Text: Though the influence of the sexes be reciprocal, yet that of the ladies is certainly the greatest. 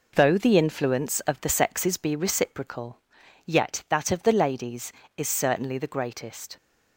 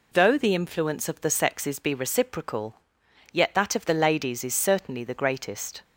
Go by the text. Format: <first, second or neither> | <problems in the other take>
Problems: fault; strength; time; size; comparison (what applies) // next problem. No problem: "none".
neither | none